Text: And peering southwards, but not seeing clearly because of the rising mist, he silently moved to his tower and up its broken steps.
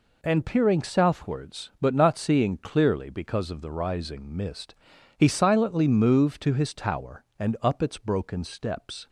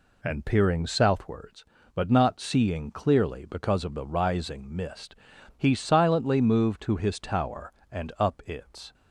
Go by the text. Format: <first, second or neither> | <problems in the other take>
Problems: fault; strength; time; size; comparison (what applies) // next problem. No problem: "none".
first | stops before "broken steps"; at 8.9 s